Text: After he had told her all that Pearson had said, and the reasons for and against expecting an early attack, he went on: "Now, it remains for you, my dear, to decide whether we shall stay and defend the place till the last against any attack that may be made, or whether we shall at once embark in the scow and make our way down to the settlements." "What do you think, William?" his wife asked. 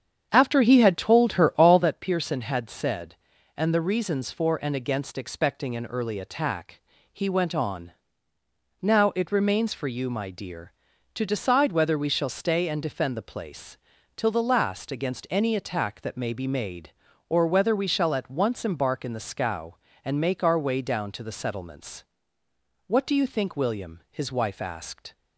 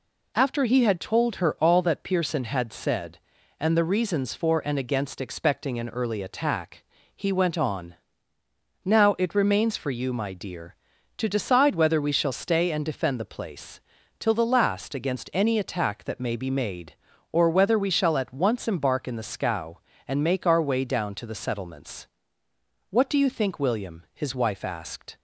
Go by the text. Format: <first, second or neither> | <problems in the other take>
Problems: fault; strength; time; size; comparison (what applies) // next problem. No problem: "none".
second | starts louder than the rest; strong; until 1.9 s; 8 dB // pauses between "place" and "till"; at 13.7 s; 0.40 s long; also in the second